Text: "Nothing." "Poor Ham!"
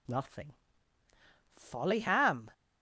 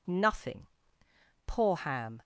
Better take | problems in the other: second | says "Folly" for "Poor"; at 1.5 s

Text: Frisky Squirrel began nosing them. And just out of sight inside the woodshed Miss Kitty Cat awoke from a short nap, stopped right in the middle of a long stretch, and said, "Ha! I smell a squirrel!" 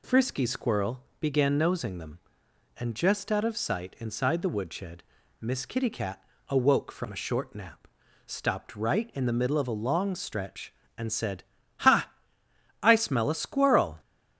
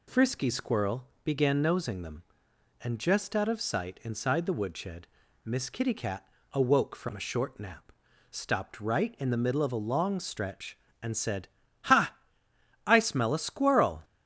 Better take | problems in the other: neither | pauses between "Squirrel" and "began"; slight; the same in both // pauses between "woodshed" and "Miss"; the same in both // pauses between "Cat" and "awoke"; slight; the same in both

